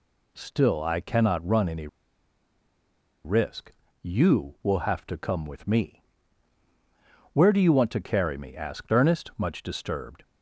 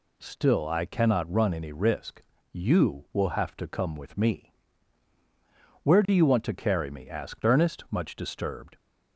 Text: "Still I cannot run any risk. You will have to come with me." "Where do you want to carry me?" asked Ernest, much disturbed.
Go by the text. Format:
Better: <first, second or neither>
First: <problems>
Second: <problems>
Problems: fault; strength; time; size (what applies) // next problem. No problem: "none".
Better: second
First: pauses between "any" and "risk"; strong; at 1.8 s; 1.3 s long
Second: none